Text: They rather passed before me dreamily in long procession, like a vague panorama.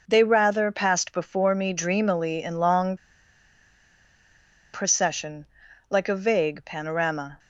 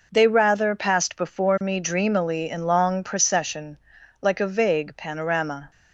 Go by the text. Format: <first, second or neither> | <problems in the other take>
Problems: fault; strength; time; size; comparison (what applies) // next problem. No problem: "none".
second | pauses between "long" and "procession"; strong; at 2.9 s; 1.7 s long